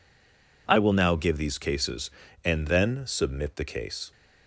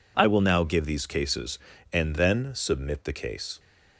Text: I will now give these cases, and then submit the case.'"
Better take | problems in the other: second | stays silent before the first word; slight; until 0.6 s; 0.6 s long

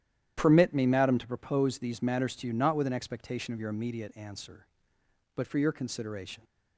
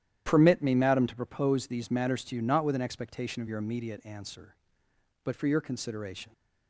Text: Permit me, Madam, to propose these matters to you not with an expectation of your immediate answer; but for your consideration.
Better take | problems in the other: neither | starts louder than the rest; strong; the same in both

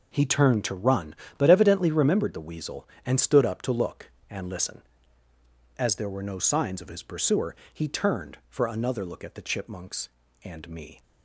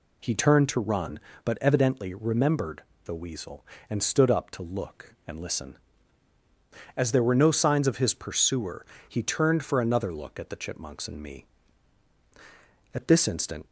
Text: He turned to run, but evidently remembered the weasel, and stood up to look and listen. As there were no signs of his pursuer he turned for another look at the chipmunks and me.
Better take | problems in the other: first | pauses between "remembered" and "the"; slight; at 2.8 s; 0.22 s long // pauses between "pursuer" and "he"; slight; at 8.8 s; 0.24 s long; slight in the first // goes on to say "At this instant"; noticeable; from 12.9 s on; 0.72 s long

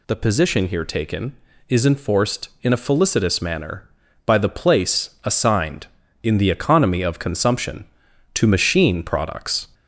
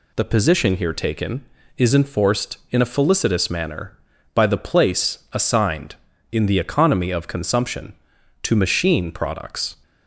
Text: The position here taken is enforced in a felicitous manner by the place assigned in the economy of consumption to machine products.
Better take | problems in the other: second | gets louder; slight; throughout; 3 dB

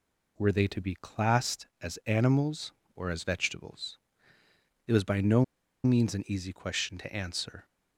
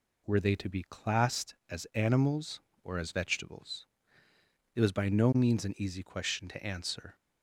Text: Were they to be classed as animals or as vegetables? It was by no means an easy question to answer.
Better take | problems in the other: second | pauses between "no" and "means"; at 5.4 s; 0.40 s long

